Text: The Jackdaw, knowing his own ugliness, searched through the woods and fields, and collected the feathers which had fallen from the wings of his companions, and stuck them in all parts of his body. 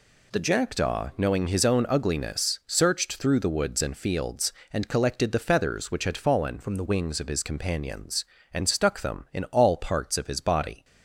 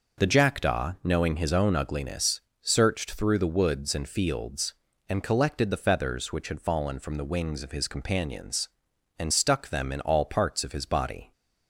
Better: second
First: changes voice from "from" to "the"; from 6.6 to 6.8 s; 0.2 s long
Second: none

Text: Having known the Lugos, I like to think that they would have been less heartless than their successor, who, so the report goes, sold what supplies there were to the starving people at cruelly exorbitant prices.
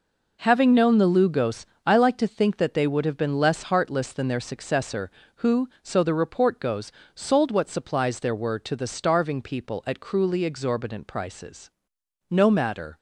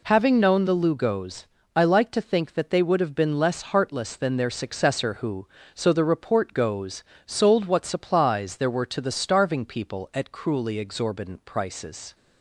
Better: second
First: goes on to say "No matter"; noticeable; from 12.2 s on; 0.68 s long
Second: none

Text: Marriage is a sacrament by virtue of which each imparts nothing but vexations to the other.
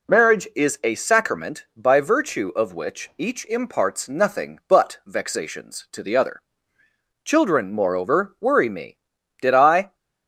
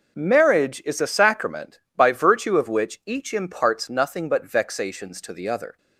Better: second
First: goes on to say "Children moreover worry me Did I"; strong; from 7.2 s on; 2.7 s long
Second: none

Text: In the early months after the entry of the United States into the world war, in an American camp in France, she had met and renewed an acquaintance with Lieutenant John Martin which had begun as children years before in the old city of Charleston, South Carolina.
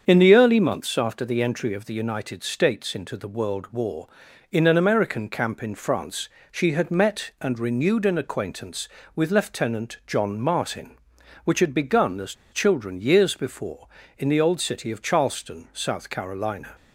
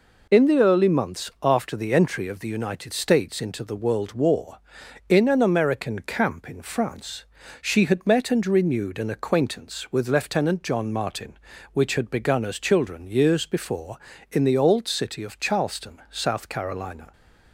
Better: second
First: starts louder than the rest; strong; until 1.0 s; 7 dB // pauses between "as" and "children"; slight; at 12.3 s; 0.18 s long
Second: none

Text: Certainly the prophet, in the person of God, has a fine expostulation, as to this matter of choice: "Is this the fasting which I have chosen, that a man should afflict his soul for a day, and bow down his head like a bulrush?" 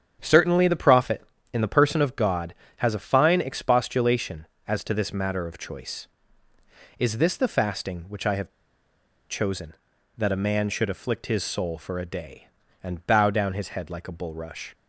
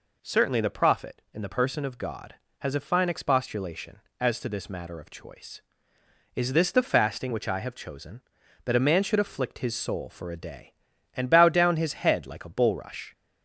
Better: second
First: starts louder than the rest; strong; until 1.2 s; 8 dB // pauses between "have" and "chosen"; noticeable; at 8.5 s; 0.79 s long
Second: none

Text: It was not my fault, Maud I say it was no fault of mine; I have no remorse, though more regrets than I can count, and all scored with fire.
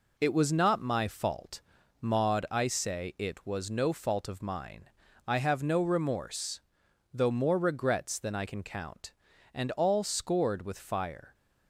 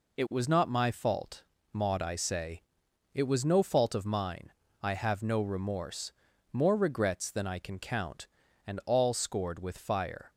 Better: first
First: none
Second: pauses between "say" and "it"; noticeable; at 2.6 s; 0.52 s long // skips "though"; at 6.3 s

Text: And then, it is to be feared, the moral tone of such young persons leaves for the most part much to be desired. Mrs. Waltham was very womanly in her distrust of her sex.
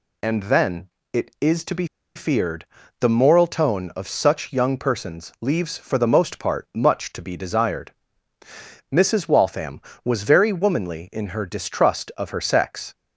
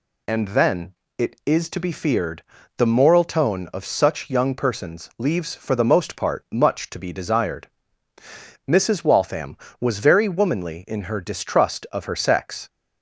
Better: second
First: pauses between "be" and "feared"; slight; at 1.8 s; 0.30 s long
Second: none

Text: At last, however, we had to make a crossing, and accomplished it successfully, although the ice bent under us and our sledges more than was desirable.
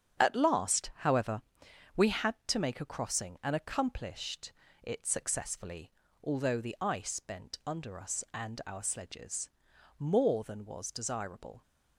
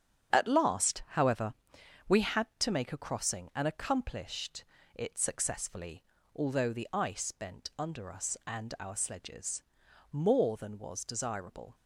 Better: neither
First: starts louder than the rest; strong; until 1.2 s; 7.5 dB // pauses between "accomplished" and "it"; slight; at 4.5 s; 0.32 s long // pauses between "sledges" and "more"; noticeable; at 9.4 s; 0.50 s long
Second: starts louder than the rest; strong; until 1.4 s; 7.5 dB // pauses between "accomplished" and "it"; slight; at 4.6 s; 0.32 s long // pauses between "sledges" and "more"; noticeable; at 9.6 s; 0.50 s long

